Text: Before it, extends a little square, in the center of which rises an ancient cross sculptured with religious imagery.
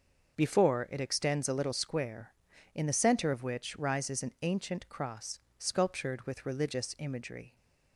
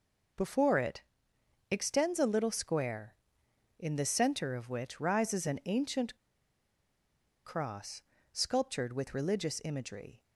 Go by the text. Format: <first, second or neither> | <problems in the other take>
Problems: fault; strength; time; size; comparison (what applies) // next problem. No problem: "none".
first | pauses between "ancient" and "cross"; strong; at 6.1 s; 1.2 s long // pauses between "cross" and "sculptured"; slight; at 8.0 s; 0.32 s long; slight in the first